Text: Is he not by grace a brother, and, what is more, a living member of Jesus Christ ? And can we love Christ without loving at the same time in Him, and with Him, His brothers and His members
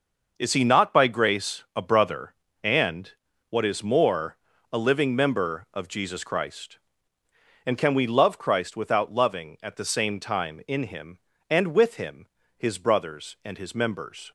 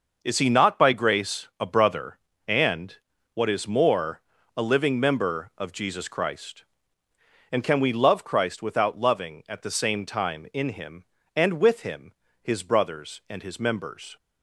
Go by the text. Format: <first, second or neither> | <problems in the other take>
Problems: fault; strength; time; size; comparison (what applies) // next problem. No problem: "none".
neither | none